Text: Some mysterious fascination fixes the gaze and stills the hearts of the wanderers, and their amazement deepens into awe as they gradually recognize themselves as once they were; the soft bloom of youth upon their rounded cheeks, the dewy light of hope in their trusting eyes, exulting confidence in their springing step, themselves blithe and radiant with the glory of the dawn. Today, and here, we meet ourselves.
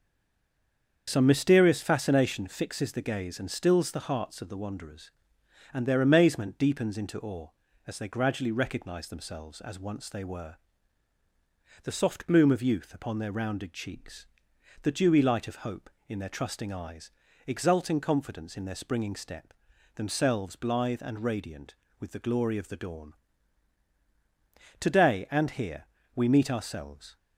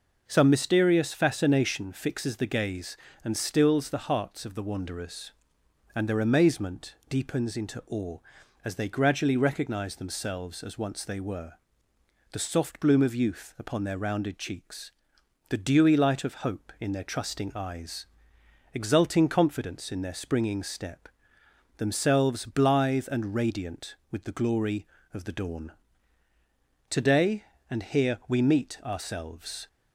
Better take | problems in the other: second | stays silent before the first word; until 1.0 s; 1.0 s long // starts louder than the rest; until 2.0 s; 7 dB

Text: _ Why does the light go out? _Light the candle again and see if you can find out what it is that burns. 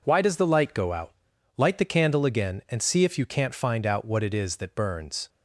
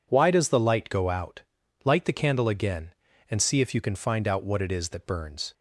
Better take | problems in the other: second | says "can't" for "can"; at 3.2 s

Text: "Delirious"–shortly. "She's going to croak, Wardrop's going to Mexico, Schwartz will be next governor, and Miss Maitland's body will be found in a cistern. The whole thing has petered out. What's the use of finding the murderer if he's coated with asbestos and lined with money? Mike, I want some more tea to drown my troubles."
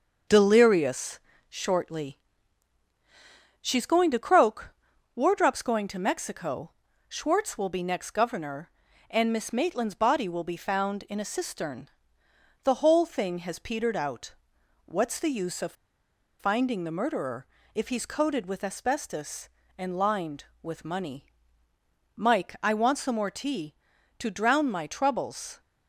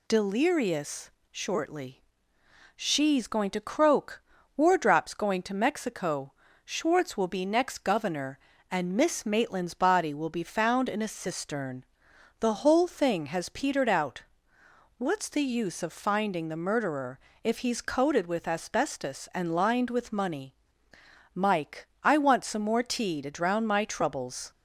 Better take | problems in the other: second | pauses between "of" and "finding"; noticeable; at 15.7 s; 0.66 s long // pauses between "murderer" and "if"; slight; at 17.4 s; 0.26 s long; slight in the second

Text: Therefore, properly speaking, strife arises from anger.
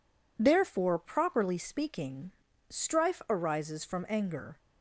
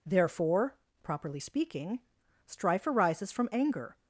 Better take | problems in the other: neither | none

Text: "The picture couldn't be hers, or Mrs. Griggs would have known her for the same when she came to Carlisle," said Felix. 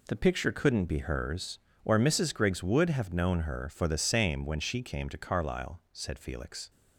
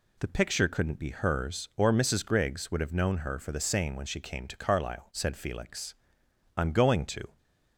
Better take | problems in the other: first | goes on to say "I'm going to"; noticeable; from 6.5 s on; 0.82 s long

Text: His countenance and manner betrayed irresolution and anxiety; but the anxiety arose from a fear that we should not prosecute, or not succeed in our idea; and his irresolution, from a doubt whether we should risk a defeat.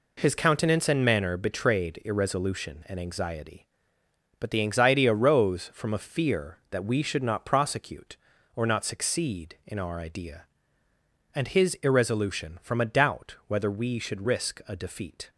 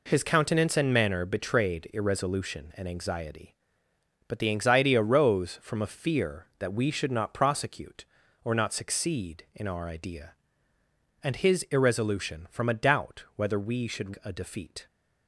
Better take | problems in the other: first | skips "risk"; at 14.1 s

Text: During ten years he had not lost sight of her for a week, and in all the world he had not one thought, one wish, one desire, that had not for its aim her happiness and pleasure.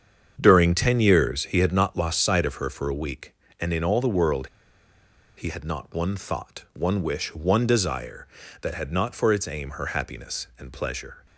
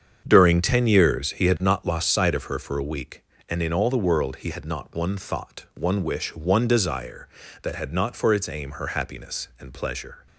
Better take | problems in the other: second | starts louder than the rest; strong; until 1.4 s; 7.5 dB; strong in the second // pauses between "world" and "he"; noticeable; at 4.4 s; 0.89 s long

